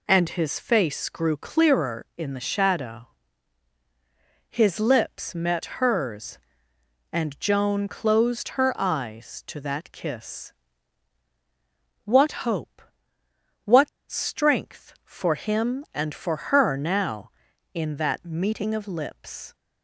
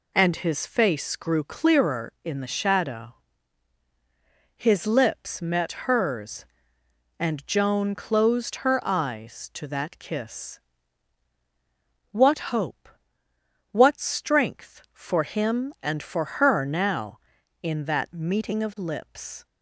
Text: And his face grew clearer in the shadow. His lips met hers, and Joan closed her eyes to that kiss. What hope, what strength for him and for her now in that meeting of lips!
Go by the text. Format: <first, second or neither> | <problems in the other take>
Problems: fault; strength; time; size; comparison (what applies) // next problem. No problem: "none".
second | pauses between "what" and "strength"; slight; at 13.8 s; 0.21 s long